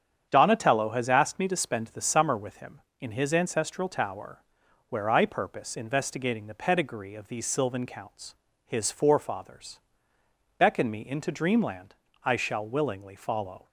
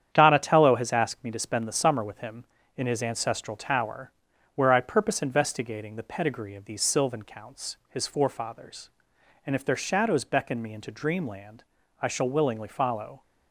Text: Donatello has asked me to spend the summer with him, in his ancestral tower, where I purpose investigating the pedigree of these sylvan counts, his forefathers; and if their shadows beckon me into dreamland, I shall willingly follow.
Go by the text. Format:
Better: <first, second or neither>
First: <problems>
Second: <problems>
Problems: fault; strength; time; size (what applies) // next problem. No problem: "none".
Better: second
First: starts louder than the rest; strong; until 1.3 s; 8 dB // skips "and if their shadows"; at 10.1 s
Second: starts louder than the rest; strong; until 1.1 s; 9 dB